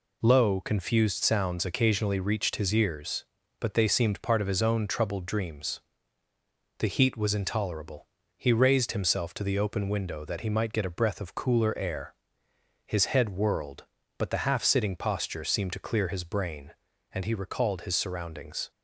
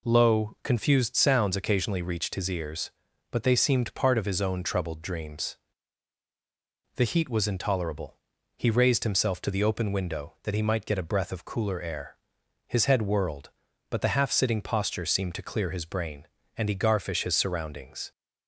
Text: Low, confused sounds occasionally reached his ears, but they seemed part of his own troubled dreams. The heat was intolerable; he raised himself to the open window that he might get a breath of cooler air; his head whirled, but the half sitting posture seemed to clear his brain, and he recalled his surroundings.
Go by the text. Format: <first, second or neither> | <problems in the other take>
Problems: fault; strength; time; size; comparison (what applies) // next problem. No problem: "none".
first | says "garfish" for "recalled"; at 16.7 s